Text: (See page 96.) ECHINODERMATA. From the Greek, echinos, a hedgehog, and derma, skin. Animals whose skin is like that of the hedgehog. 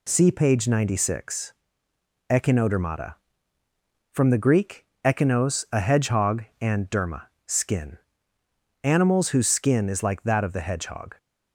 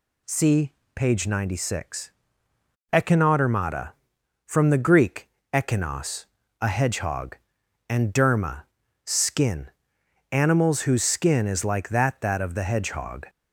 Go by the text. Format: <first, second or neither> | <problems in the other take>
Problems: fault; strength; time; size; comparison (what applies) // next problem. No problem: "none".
first | pauses between "See" and "page"; slight; at 0.7 s; 0.24 s long // says "that" twice; at 12.2 s